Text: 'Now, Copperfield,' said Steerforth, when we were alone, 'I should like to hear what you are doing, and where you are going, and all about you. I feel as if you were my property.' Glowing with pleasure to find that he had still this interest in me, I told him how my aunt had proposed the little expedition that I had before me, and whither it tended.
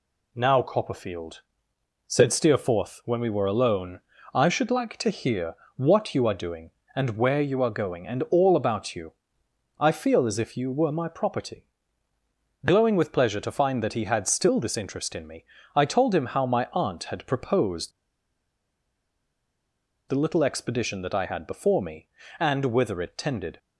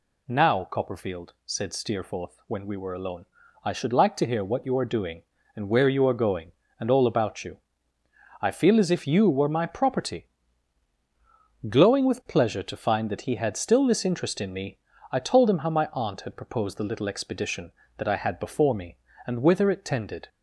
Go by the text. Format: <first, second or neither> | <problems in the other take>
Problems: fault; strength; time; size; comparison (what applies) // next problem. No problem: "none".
second | pauses between "hear" and "what"; slight; at 5.5 s; 0.20 s long // pauses between "proposed" and "the"; strong; at 17.9 s; 2.1 s long